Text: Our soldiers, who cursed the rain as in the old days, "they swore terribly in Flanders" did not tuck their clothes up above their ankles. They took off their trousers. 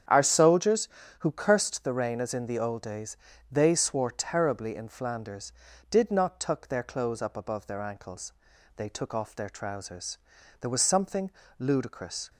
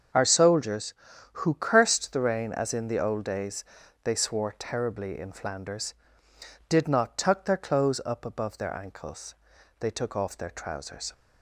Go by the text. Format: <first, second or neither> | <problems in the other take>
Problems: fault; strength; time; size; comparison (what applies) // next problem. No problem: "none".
second | starts louder than the rest; strong; until 1.4 s; 8.5 dB; also in the second // goes on to say "There was something ludicrous"; strong; from 10.5 s on; 1.7 s long